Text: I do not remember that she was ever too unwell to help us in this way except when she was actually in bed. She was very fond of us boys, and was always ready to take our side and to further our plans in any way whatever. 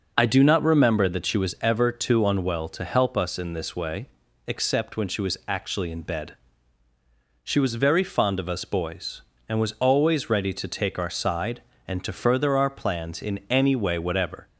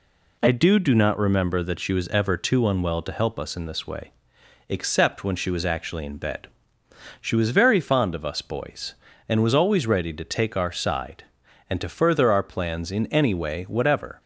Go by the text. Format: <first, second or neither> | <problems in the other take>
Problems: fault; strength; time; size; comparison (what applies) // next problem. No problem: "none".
first | says "do" twice; at 0.7 s // pauses between "way" and "except"; noticeable; at 4.1 s; 0.58 s long; also in the first